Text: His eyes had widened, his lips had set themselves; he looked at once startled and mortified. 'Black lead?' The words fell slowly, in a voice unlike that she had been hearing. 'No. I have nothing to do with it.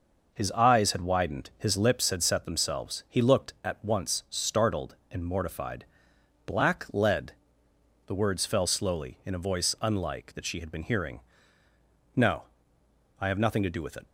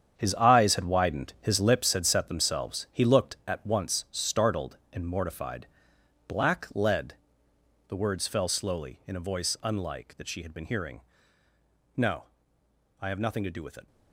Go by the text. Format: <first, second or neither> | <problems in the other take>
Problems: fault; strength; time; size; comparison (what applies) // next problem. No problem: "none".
first | gets quieter; strong; throughout; 10.5 dB